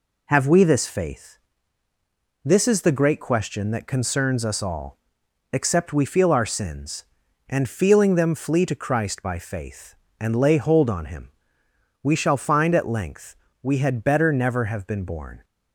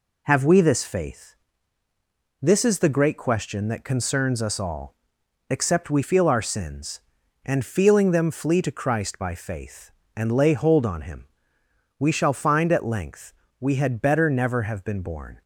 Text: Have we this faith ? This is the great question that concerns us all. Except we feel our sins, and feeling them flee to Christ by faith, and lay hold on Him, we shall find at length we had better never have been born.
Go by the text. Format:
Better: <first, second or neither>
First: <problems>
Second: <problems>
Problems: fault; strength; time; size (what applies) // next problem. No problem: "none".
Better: neither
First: pauses between "length" and "we"; slight; at 13.3 s; 0.26 s long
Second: pauses between "length" and "we"; slight; at 13.3 s; 0.26 s long